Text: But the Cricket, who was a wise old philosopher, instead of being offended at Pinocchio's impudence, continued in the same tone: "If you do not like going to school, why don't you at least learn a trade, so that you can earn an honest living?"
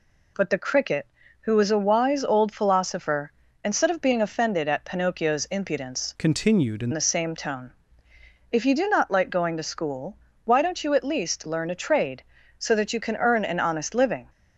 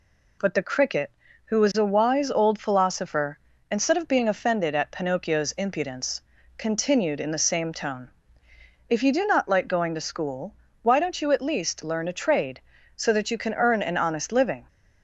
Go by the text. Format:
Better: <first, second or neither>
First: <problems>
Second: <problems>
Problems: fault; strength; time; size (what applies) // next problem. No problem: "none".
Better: second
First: changes voice from "continued" to "in"; from 6.1 to 6.9 s; 0.8 s long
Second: none